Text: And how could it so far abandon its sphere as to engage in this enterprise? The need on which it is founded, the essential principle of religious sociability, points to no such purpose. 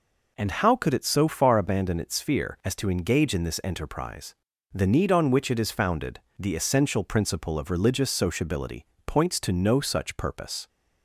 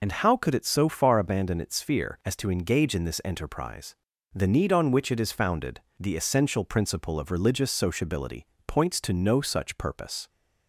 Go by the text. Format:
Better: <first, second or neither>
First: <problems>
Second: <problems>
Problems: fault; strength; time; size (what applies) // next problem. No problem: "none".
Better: first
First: none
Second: loses the start of "And"; at 0.0 s; 50 ms